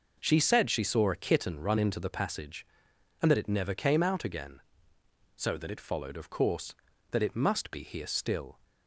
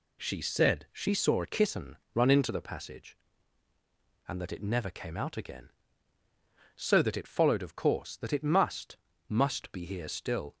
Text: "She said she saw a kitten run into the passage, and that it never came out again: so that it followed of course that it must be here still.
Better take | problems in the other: first | pauses between "kitten" and "run"; slight; at 1.9 s; 0.18 s long // says "must" twice; at 9.2 s

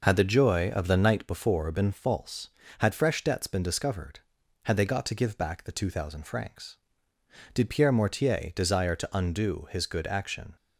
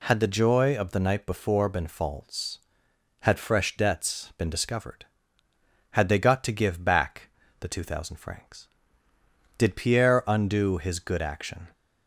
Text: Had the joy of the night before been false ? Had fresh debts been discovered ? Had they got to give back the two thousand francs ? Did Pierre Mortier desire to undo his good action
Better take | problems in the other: first | pauses between "back" and "the"; slight; at 7.2 s; 0.32 s long // skips "Mortier desire to"; at 10.2 s

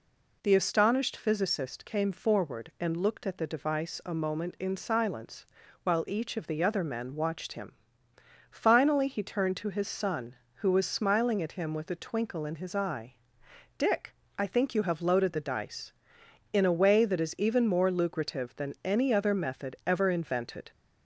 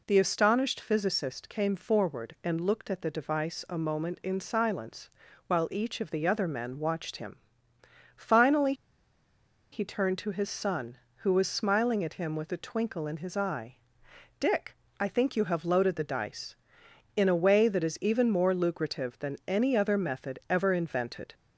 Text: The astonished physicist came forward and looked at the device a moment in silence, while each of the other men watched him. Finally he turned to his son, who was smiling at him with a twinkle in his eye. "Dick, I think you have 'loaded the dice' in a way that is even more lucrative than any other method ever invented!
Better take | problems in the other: first | pauses between "Finally" and "he"; at 8.7 s; 0.98 s long

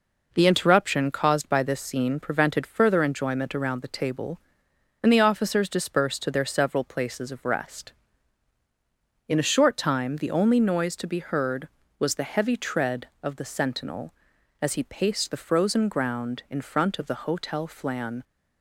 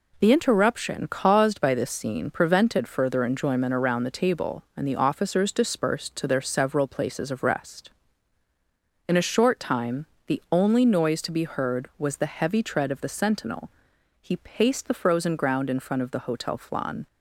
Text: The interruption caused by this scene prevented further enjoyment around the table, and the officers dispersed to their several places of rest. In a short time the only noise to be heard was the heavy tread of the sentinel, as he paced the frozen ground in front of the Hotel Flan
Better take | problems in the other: first | pauses between "time" and "the"; slight; at 10.0 s; 0.20 s long // skips "as"; at 13.9 s

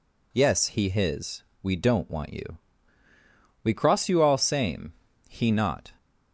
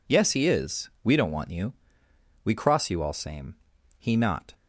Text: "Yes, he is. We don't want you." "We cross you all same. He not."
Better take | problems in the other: second | says "his" for "is"; at 0.9 s

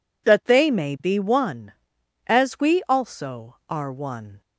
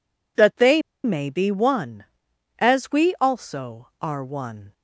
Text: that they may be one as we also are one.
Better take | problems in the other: first | pauses between "they" and "may"; slight; at 0.8 s; 0.23 s long

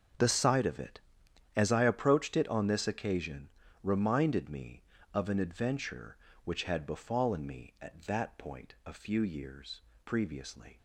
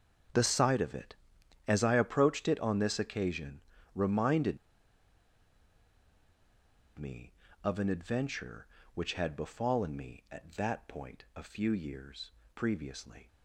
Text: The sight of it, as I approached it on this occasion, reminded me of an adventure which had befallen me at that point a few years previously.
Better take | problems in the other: first | starts louder than the rest; until 1.8 s; 7 dB; also in the first // pauses between "reminded" and "me"; strong; at 4.5 s; 2.4 s long // pauses between "years" and "previously"; slight; at 12.3 s; 0.22 s long; slight in the first

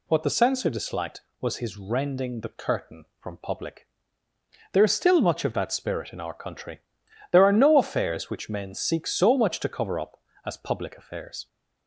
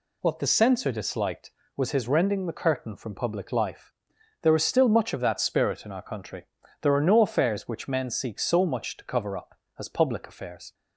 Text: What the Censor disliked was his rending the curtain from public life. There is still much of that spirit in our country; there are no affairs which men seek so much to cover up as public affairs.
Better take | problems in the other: second | skips "life"; at 4.2 s

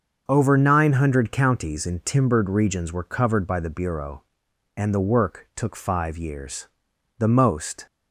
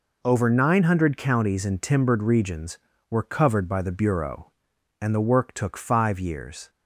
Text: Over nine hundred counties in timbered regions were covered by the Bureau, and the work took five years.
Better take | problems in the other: second | starts louder than the rest; until 1.2 s; 6.5 dB // goes on to say "The most"; noticeable; from 7.1 s on; 0.66 s long

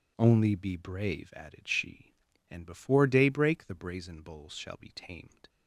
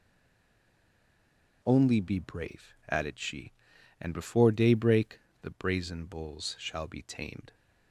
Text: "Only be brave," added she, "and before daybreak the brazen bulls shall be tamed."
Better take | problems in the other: first | stays silent before the first word; noticeable; until 1.6 s; 1.6 s long // pauses between "daybreak" and "the"; slight; at 5.1 s; 0.21 s long

